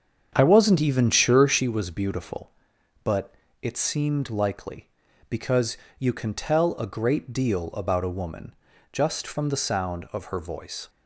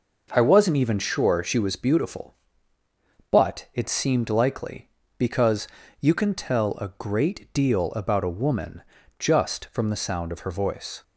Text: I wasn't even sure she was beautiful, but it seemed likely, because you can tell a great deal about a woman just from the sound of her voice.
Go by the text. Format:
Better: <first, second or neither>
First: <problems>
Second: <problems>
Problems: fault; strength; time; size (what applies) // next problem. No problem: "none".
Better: second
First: starts louder than the rest; strong; until 1.7 s; 7.5 dB // pauses between "but" and "it"; slight; at 3.3 s; 0.30 s long // pauses between "because" and "you"; slight; at 5.7 s; 0.22 s long // pauses between "woman" and "just"; slight; at 8.5 s; 0.36 s long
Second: pauses between "because" and "you"; slight; at 5.6 s; 0.31 s long // pauses between "woman" and "just"; slight; at 8.8 s; 0.36 s long